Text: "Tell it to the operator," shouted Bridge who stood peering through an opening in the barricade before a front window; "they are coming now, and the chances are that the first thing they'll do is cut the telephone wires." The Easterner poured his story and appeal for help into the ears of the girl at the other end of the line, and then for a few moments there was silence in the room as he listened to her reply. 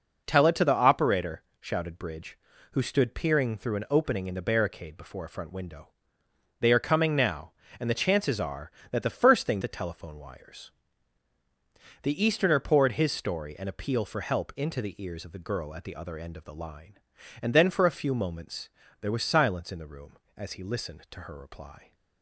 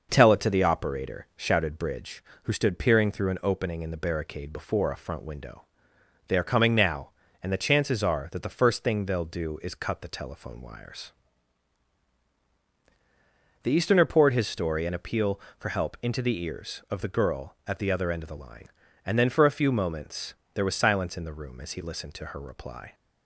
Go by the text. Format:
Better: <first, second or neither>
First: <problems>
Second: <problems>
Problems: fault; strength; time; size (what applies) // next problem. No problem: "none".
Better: second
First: skips "they'll do is cut"; at 9.6 s // pauses between "moments" and "there"; slight; at 18.6 s; 0.32 s long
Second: pauses between "moments" and "there"; slight; at 20.3 s; 0.22 s long